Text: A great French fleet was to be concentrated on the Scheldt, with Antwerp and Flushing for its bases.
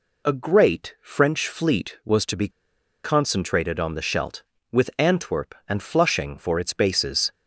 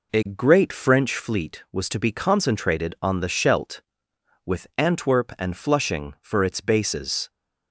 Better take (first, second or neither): second